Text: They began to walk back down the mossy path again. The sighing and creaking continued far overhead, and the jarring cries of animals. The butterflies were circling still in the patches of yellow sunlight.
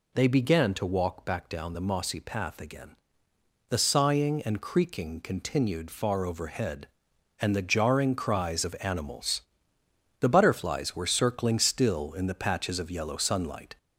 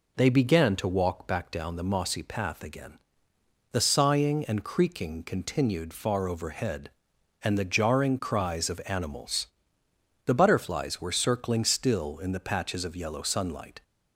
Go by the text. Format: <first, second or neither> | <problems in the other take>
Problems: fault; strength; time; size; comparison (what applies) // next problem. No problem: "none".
second | gets louder; slight; throughout; 2.5 dB